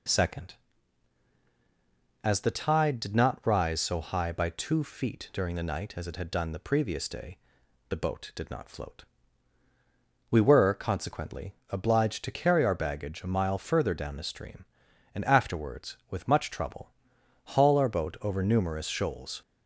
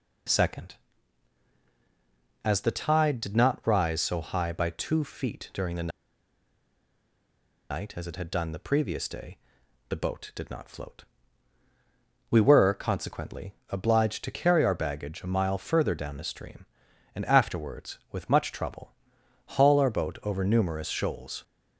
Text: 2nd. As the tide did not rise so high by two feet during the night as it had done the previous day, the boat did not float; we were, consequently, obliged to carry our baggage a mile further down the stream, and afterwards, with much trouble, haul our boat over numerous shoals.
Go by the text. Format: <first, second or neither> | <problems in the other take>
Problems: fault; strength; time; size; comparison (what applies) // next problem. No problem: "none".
first | pauses between "the" and "night"; strong; at 5.8 s; 1.8 s long